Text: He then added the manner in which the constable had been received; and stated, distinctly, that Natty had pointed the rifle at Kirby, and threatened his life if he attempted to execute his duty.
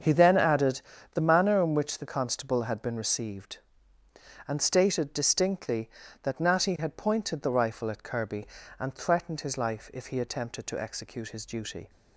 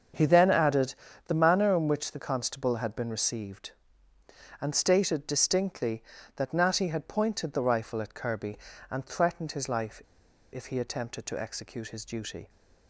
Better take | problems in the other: first | starts louder than the rest; until 1.4 s; 7 dB; also in the first // pauses between "added" and "the"; slight; at 0.9 s; 0.32 s long; slight in the first // pauses between "life" and "if"; noticeable; at 10.0 s; 0.52 s long

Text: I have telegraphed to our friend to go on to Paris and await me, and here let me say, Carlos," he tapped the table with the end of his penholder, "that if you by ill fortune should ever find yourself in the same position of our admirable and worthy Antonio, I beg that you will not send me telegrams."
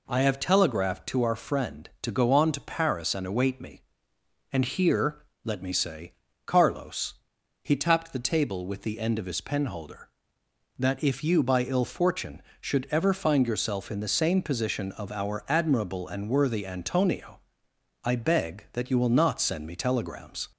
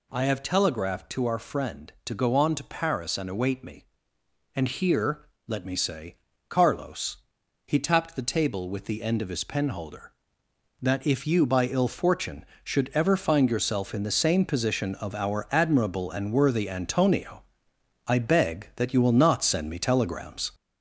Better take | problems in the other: first | gets louder; throughout; 4 dB // pauses between "here" and "let"; slight; at 5.2 s; 0.20 s long; slight in the first

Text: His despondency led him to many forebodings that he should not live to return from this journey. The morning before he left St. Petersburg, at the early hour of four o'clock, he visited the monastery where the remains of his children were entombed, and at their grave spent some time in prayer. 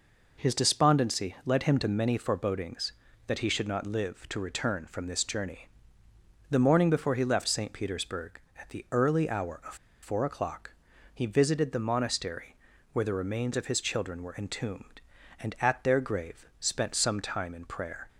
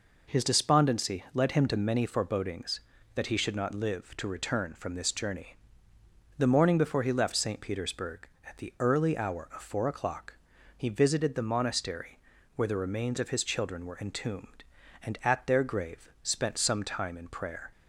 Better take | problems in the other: second | pauses between "of" and "four"; slight; at 9.7 s; 0.27 s long // pauses between "monastery" and "where"; at 12.5 s; 0.38 s long; also in the second // pauses between "grave" and "spent"; slight; at 16.4 s; 0.16 s long; slight in the second

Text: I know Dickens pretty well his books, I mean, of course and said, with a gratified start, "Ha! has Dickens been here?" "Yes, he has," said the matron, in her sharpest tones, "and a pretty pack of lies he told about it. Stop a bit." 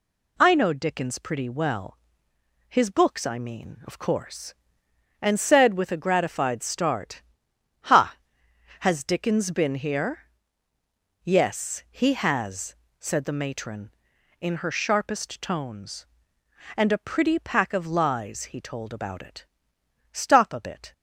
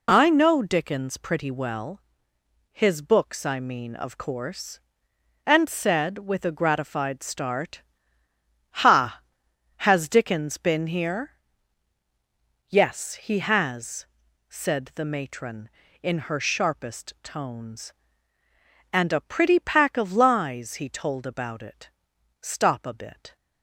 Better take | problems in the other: neither | pauses between "well" and "his"; noticeable; the same in both

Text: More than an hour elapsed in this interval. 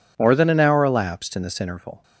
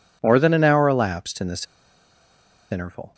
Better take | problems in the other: first | pauses between "this" and "interval"; at 1.6 s; 1.0 s long

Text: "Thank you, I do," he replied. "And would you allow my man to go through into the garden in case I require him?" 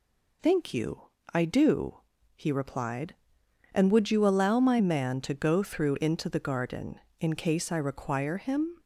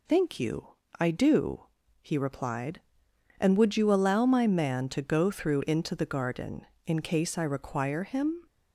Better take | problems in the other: neither | none

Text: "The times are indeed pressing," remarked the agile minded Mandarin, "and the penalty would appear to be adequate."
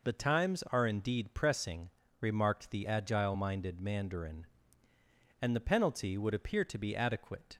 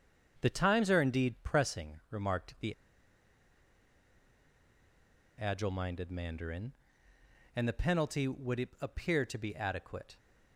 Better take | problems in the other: first | starts louder than the rest; until 1.4 s; 7 dB // pauses between "the" and "agile"; strong; at 2.7 s; 2.6 s long

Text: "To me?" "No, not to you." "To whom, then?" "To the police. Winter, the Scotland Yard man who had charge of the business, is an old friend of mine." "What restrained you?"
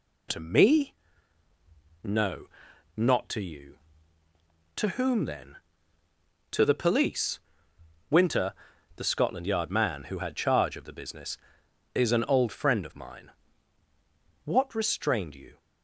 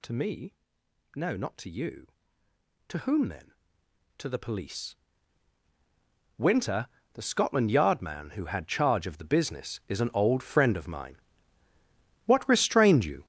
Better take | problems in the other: first | gets louder; strong; throughout; 11 dB

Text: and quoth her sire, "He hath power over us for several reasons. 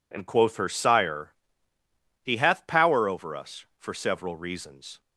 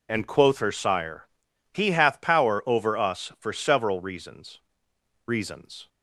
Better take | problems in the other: first | says "reasons" twice; at 5.2 s

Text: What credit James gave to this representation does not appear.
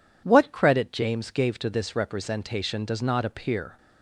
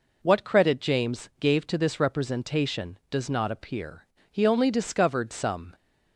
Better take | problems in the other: first | goes on to say "He only discovered some"; from 4.3 s on; 1.4 s long

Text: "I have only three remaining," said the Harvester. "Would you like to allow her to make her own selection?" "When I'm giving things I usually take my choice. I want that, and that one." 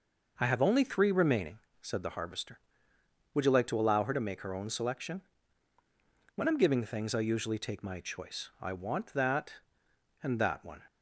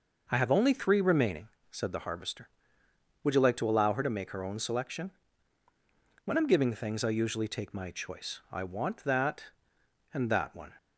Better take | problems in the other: neither | none

